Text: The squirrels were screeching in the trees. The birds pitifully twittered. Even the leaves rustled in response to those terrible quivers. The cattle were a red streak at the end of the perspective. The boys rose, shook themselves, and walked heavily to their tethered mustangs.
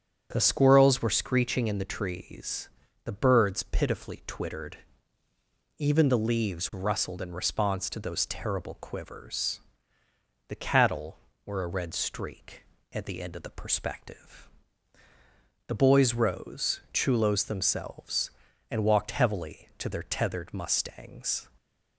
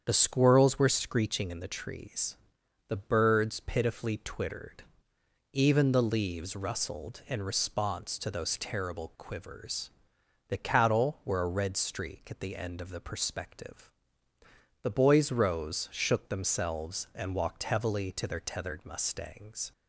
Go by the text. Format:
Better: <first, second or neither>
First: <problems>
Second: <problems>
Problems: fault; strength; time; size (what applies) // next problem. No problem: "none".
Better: second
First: starts louder than the rest; strong; until 1.3 s; 8 dB // says "chulos" for "shook"; at 16.9 s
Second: starts louder than the rest; strong; until 1.0 s; 8 dB